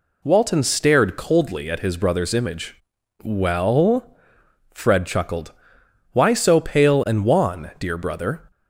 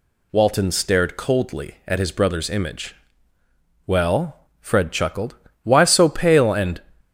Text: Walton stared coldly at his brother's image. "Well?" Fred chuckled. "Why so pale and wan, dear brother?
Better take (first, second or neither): first